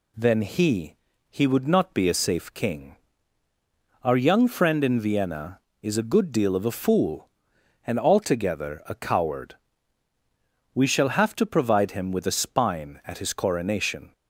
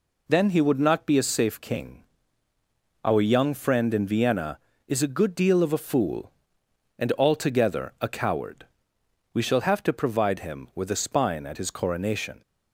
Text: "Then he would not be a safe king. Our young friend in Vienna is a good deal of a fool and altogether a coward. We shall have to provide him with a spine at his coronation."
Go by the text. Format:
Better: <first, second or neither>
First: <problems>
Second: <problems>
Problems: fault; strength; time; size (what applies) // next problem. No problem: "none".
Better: second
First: says "he" twice; at 1.2 s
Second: none